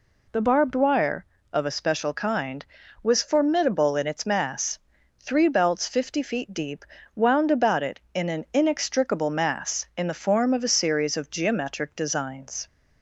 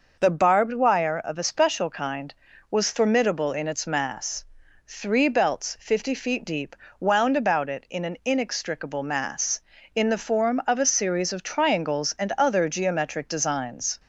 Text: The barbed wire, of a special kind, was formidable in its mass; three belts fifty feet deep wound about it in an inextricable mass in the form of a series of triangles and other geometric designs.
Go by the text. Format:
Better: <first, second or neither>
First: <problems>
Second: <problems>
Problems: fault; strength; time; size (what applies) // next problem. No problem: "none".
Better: second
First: pauses between "deep" and "wound"; slight; at 6.8 s; 0.30 s long // skips "triangles and other"; at 11.3 s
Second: pauses between "deep" and "wound"; slight; at 6.7 s; 0.24 s long